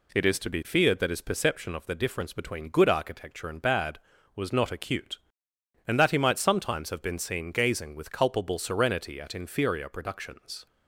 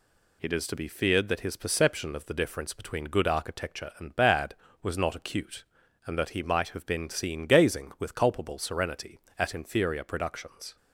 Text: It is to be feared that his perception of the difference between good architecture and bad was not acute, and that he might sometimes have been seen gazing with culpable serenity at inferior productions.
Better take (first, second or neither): first